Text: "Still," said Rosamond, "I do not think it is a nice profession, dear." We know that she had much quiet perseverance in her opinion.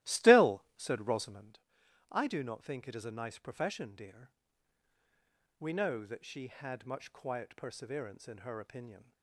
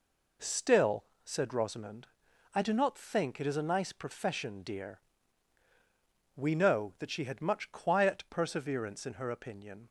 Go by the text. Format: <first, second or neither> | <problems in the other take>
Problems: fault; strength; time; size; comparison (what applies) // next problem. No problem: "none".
second | starts louder than the rest; strong; until 1.5 s; 15.5 dB